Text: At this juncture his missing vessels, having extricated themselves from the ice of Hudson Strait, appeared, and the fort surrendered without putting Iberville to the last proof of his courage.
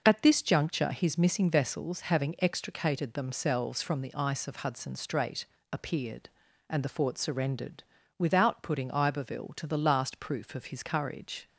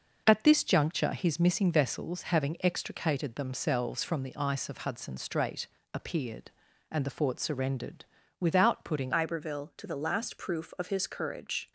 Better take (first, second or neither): first